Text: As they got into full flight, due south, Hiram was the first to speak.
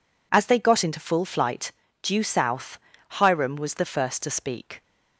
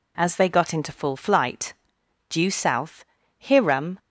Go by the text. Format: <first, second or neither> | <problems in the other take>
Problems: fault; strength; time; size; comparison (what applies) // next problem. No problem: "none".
first | stops before "was the first to speak"; at 3.9 s